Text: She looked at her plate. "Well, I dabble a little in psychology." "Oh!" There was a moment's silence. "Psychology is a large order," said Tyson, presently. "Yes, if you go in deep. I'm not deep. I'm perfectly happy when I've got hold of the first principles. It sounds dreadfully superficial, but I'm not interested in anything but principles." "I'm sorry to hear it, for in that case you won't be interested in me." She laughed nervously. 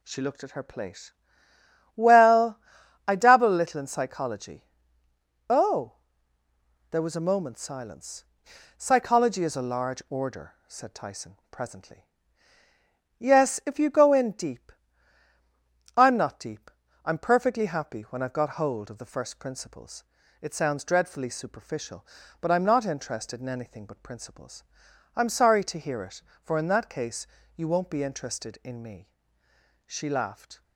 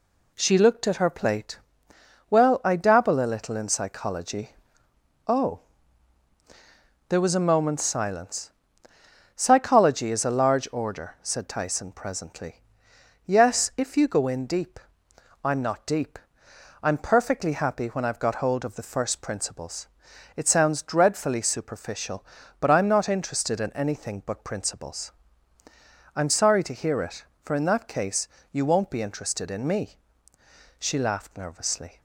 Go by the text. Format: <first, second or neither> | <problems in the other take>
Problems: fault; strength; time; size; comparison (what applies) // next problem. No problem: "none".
second | pauses between "case" and "you"; slight; at 27.2 s; 0.28 s long; slight in the second // stops before "nervously"; at 30.6 s